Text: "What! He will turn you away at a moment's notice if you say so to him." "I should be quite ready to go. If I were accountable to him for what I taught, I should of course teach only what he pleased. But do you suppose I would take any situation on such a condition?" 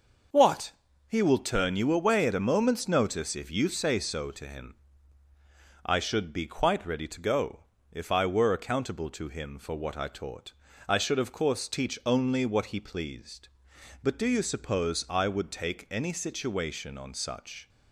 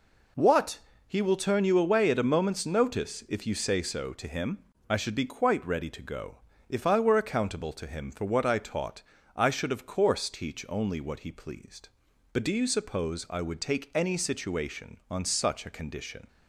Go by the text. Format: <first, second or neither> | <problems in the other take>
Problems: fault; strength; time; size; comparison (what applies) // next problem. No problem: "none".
second | starts louder than the rest; until 1.7 s; 6 dB // stops before "a condition"; at 17.6 s